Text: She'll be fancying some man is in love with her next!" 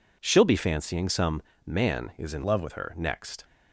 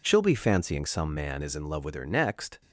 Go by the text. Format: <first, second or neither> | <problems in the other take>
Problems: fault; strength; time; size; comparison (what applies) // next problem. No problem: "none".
second | pauses between "some" and "man"; slight; at 1.4 s; 0.24 s long // changes voice from "love" to "with"; from 2.4 to 2.7 s; 0.3 s long